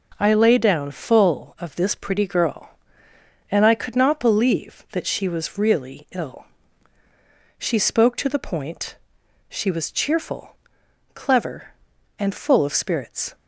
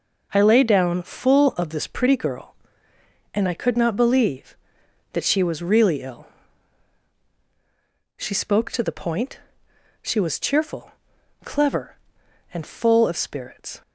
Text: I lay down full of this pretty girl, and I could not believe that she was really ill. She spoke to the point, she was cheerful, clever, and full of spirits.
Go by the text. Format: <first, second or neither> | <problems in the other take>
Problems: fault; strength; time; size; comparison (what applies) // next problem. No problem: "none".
neither | none